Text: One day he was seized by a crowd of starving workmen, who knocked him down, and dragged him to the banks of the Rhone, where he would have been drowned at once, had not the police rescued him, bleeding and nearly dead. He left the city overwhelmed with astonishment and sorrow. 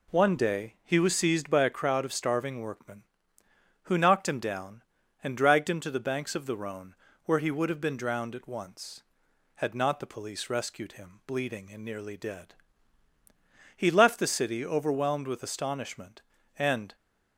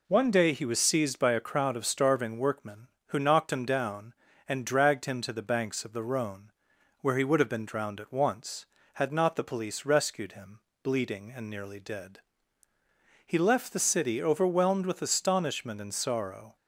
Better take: second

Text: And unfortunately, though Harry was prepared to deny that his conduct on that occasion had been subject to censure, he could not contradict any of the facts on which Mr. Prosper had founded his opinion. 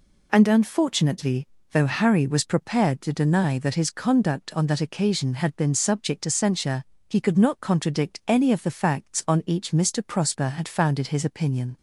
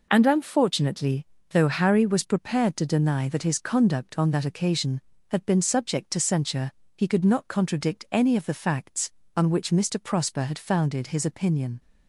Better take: second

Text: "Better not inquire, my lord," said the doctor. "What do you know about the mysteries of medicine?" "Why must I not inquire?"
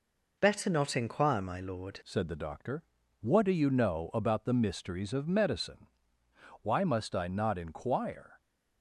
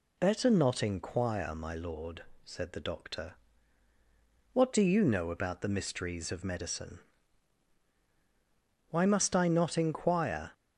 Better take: second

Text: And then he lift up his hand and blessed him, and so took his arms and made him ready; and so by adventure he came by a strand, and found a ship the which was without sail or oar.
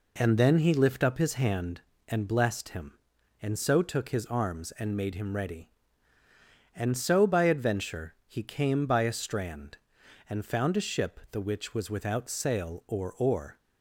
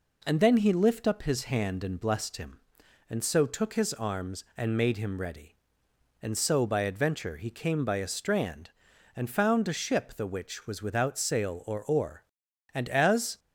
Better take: first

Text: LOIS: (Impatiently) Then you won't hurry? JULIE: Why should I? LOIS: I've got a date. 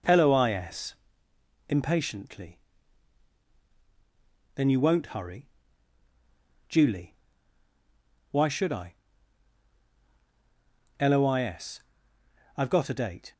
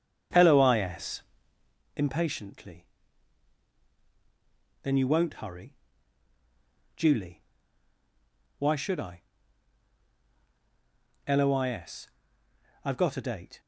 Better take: first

